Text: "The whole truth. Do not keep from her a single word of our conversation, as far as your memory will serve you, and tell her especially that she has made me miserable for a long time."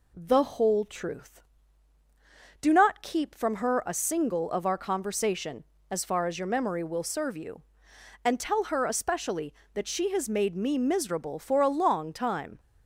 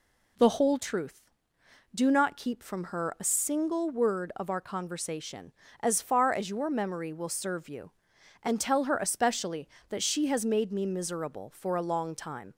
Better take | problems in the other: second | skips "word"; at 4.5 s

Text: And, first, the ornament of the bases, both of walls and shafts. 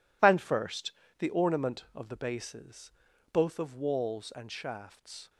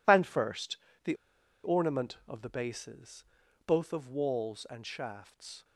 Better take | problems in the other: first | pauses between "the" and "ornament"; noticeable; at 1.1 s; 0.49 s long

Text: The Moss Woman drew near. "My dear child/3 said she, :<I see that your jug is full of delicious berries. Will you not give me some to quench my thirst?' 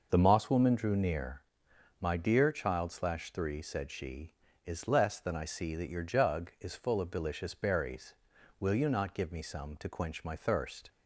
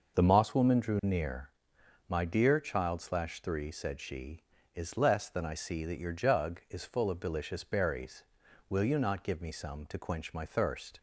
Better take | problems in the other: neither | none

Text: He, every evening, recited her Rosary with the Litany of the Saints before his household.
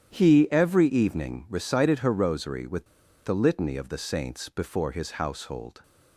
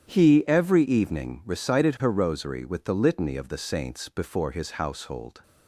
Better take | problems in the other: second | starts louder than the rest; strong; until 1.2 s; 10 dB; strong in the second // pauses between "with" and "the"; at 2.8 s; 0.39 s long

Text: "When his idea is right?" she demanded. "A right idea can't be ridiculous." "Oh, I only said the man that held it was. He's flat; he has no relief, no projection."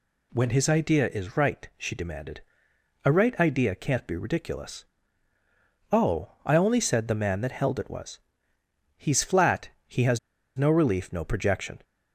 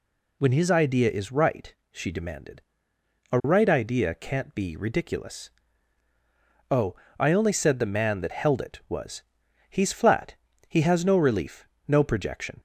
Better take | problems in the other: second | pauses between "has" and "no"; at 10.1 s; 0.38 s long

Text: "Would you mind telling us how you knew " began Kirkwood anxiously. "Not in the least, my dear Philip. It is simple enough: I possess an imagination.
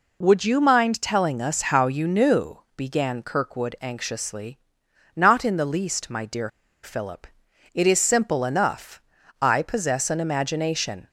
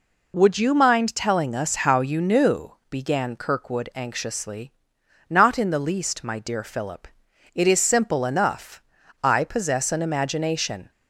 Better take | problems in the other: second | pauses between "dear" and "Philip"; slight; at 6.4 s; 0.35 s long

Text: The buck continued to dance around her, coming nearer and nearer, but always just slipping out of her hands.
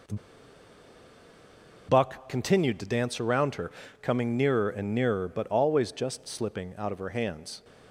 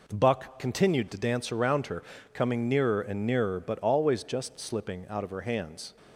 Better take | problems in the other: second | pauses between "The" and "buck"; strong; at 0.1 s; 1.7 s long

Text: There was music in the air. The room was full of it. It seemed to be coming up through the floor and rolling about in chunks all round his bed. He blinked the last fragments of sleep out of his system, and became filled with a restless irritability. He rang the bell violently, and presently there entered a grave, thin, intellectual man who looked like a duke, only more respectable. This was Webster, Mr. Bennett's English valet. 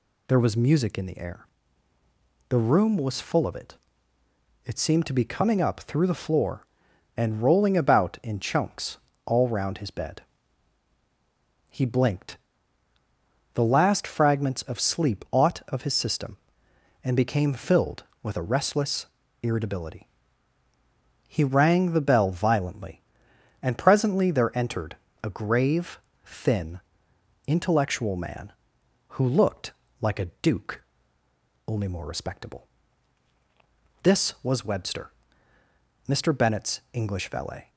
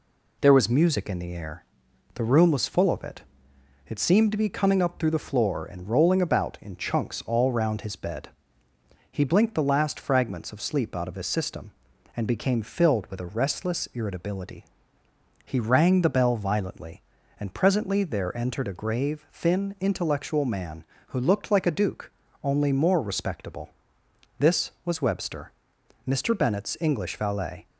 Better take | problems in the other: second | pauses between "chunks" and "all"; slight; at 8.9 s; 0.30 s long // pauses between "blinked" and "the"; at 12.3 s; 1.1 s long // says "ought" for "out"; at 15.3 s // pauses between "restless" and "irritability"; at 19.0 s; 0.38 s long // pauses between "entered" and "a"; slight; at 24.9 s; 0.26 s long // pauses between "looked" and "like"; slight; at 29.7 s; 0.30 s long

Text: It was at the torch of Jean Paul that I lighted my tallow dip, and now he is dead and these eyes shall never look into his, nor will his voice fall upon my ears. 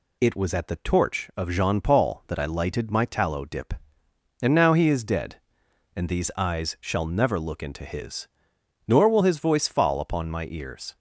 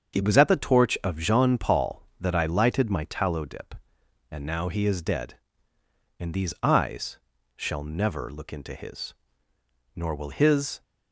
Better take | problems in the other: first | starts louder than the rest; until 1.1 s; 7 dB // pauses between "eyes" and "shall"; at 7.1 s; 0.40 s long // stops before "voice fall upon my ears"; at 10.8 s

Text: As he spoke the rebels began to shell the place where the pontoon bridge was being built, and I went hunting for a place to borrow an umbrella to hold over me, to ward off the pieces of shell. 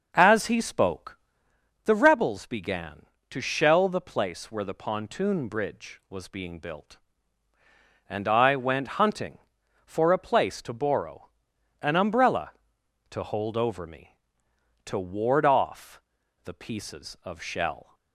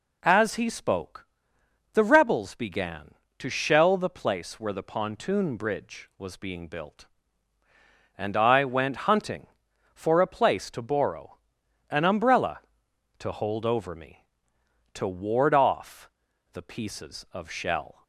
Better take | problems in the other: second | starts louder than the rest; noticeable; until 1.5 s; 6 dB // pauses between "spoke" and "the"; noticeable; at 1.1 s; 0.68 s long; noticeable in the second // pauses between "borrow" and "an"; noticeable; at 11.3 s; 0.50 s long; noticeable in the second // pauses between "off" and "the"; at 16.0 s; 0.42 s long; also in the second

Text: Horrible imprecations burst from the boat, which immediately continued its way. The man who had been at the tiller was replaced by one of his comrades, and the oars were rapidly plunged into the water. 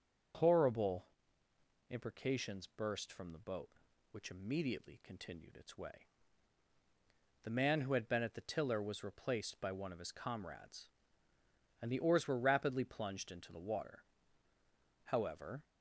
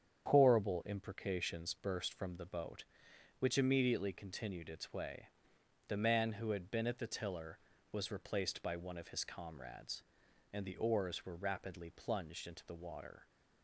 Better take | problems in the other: second | starts louder than the rest; until 2.2 s; 7 dB; strong in the second // pauses between "Horrible" and "imprecations"; noticeable; at 1.0 s; 0.84 s long // goes on to say "However"; from 15.0 s on; 0.58 s long

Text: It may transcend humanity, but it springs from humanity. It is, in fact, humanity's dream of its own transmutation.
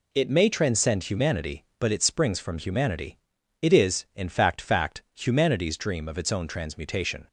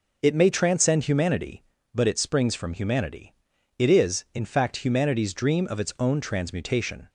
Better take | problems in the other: second | says "fact" twice; at 4.5 s

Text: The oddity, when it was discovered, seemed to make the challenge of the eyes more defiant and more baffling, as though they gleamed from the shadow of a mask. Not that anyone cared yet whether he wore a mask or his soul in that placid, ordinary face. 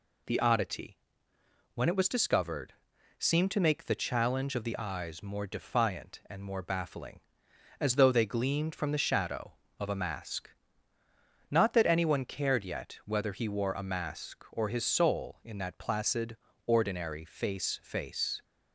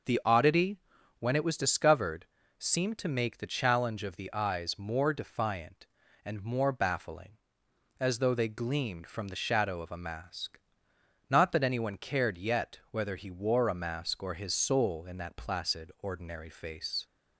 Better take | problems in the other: second | says "face" twice; at 17.8 s

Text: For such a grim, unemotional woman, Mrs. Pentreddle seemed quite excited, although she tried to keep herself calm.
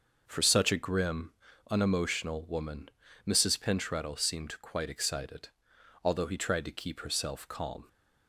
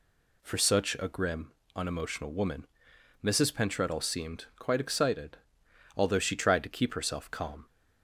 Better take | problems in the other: second | starts louder than the rest; until 1.2 s; 6 dB // says "he" for "she"; at 6.2 s

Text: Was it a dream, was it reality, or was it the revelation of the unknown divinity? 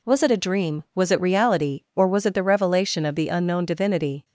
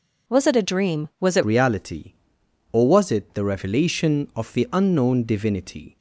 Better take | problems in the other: first | changes voice at "reality"; from 1.4 s on; 4.5 s long

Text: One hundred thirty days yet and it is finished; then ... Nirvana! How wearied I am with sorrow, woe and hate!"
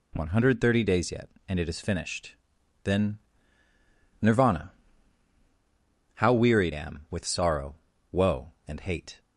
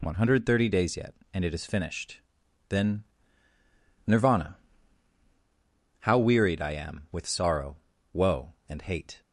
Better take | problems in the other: second | skips "I"; at 6.7 s

